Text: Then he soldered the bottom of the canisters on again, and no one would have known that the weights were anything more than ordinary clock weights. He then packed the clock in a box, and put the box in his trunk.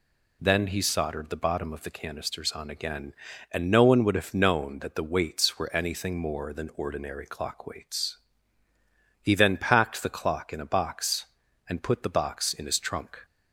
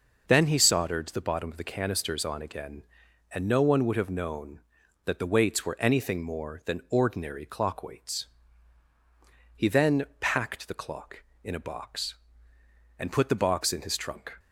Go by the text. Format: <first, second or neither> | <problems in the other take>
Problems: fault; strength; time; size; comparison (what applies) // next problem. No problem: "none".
neither | none